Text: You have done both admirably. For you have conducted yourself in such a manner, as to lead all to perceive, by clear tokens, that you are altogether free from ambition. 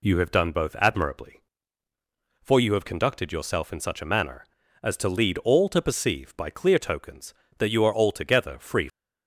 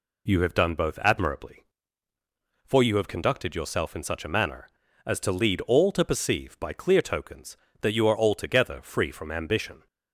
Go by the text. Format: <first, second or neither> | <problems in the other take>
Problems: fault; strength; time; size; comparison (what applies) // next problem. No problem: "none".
second | stops before "from ambition"; at 8.8 s